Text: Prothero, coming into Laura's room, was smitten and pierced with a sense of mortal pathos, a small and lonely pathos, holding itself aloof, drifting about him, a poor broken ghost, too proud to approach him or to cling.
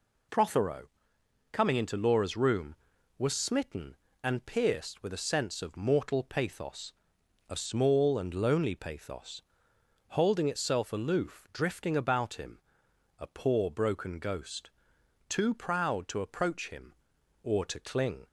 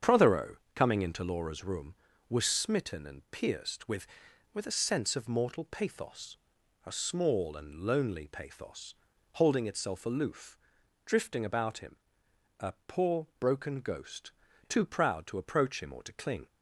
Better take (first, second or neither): first